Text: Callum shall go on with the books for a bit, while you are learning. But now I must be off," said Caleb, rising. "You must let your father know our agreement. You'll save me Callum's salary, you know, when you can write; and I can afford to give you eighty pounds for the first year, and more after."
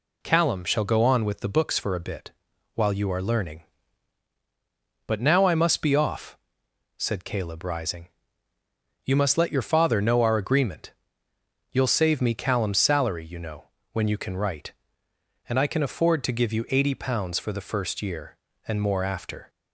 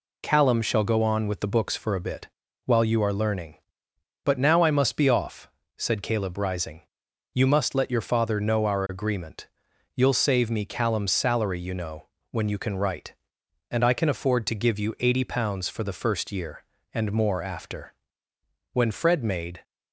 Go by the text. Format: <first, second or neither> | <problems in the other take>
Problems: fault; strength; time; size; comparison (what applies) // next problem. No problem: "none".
first | goes on to say "When Fred made"; noticeable; from 18.7 s on; 0.90 s long